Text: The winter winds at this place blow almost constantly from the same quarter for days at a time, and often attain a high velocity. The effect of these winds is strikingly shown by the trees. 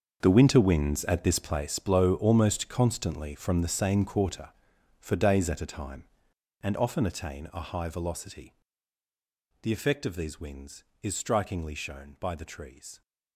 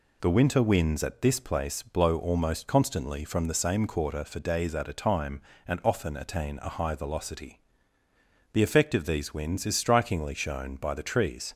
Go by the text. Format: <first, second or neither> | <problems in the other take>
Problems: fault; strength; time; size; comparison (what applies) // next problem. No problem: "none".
second | gets quieter; strong; throughout; 14 dB